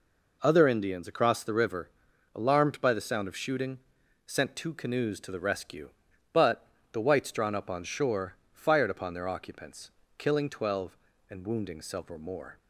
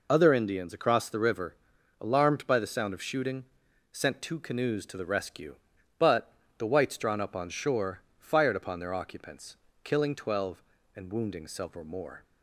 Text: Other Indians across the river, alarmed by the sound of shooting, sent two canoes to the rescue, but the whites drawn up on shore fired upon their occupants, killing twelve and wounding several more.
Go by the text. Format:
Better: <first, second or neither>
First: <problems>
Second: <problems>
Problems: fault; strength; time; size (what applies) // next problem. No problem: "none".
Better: first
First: pauses between "but" and "the"; slight; at 6.6 s; 0.24 s long // pauses between "shore" and "fired"; slight; at 8.3 s; 0.18 s long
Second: loses the start of "Other"; at 0.0 s; 30 ms // pauses between "but" and "the"; slight; at 6.3 s; 0.24 s long // pauses between "shore" and "fired"; slight; at 8.0 s; 0.18 s long